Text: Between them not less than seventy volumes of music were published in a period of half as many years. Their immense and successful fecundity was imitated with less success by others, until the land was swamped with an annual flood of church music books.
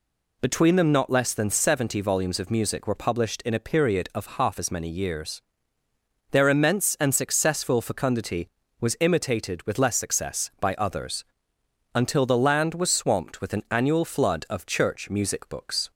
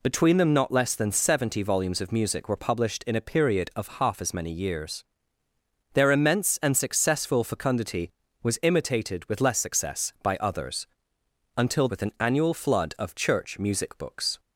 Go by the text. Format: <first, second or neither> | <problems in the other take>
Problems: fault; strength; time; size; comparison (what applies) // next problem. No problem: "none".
first | skips "the land was swamped"; at 11.8 s